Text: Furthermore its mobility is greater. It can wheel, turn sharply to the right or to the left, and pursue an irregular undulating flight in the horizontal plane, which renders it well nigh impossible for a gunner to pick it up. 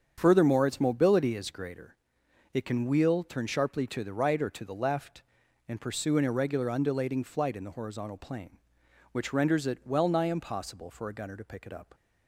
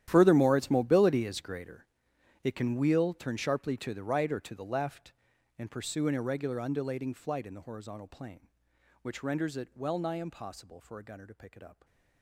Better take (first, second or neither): first